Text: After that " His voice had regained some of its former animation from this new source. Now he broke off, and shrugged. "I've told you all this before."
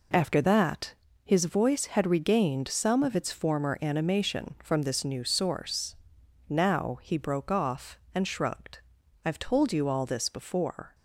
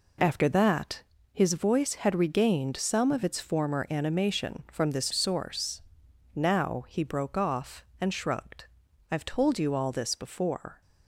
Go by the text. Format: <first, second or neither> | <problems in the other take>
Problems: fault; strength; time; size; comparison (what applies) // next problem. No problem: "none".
first | skips "new"; at 5.1 s